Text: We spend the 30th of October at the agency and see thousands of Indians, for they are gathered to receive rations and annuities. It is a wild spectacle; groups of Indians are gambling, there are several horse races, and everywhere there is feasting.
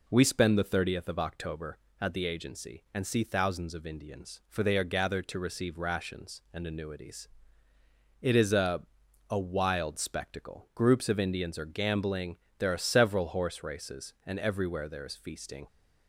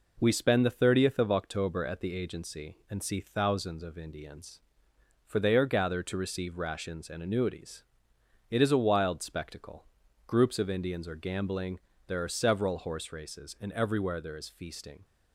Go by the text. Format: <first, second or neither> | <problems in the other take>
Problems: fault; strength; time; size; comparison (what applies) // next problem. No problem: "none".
second | says "a" twice; at 9.2 s